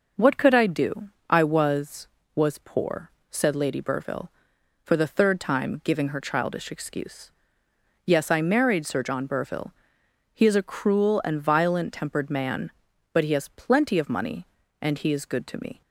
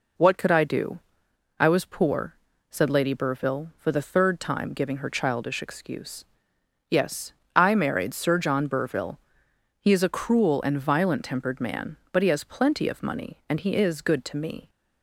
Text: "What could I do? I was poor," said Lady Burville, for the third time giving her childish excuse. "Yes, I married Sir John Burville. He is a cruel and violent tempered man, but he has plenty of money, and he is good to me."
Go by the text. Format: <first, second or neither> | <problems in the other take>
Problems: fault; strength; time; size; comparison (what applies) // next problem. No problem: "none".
second | says "was" twice; at 2.3 s